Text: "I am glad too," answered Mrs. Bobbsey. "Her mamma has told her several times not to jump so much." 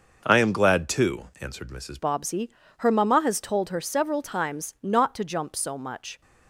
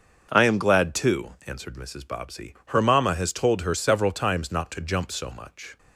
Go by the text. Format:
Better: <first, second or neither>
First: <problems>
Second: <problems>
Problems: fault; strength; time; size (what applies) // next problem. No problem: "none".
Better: second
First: starts louder than the rest; noticeable; until 1.2 s; 6 dB // changes voice at "Bobbsey"; from 1.9 s on; 4.3 s long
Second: starts louder than the rest; until 1.3 s; 6.5 dB